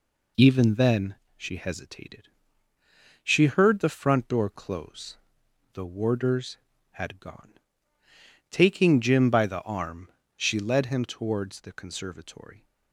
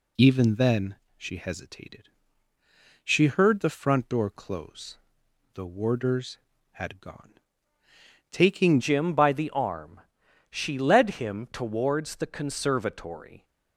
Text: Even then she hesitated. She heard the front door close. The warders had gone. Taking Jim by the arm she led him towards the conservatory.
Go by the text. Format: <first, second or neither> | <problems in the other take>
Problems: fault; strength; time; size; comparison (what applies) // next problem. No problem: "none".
first | pauses between "then" and "she"; slight; at 0.9 s; 0.22 s long; slight in the first // changes voice at "Jim"; from 8.7 s on; 4.7 s long // pauses between "arm" and "she"; noticeable; at 10.0 s; 0.50 s long; slight in the first